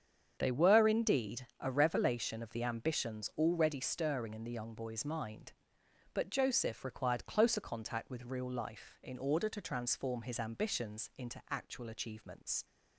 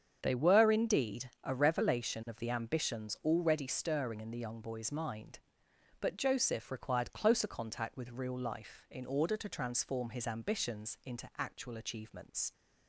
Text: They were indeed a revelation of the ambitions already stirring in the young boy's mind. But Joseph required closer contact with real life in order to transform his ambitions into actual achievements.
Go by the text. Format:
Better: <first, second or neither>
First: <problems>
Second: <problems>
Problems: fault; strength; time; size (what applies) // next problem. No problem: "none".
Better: neither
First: starts louder than the rest; strong; until 1.4 s; 7.5 dB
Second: starts louder than the rest; strong; until 1.2 s; 7.5 dB